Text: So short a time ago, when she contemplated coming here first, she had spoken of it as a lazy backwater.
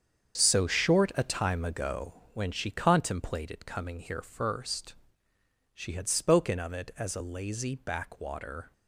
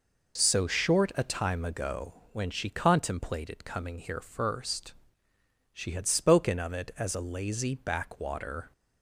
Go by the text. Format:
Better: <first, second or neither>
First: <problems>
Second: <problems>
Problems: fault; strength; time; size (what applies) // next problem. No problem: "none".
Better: second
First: gets quieter; strong; throughout; 11 dB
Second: none